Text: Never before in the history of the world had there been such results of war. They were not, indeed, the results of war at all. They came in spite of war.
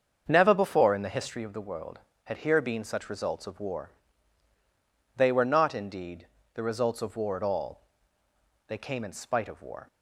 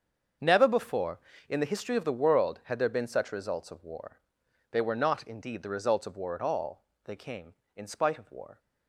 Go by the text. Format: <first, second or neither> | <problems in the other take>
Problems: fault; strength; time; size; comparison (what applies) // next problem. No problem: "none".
second | starts louder than the rest; until 1.2 s; 7 dB; also in the second // says "here" for "there"; at 2.3 s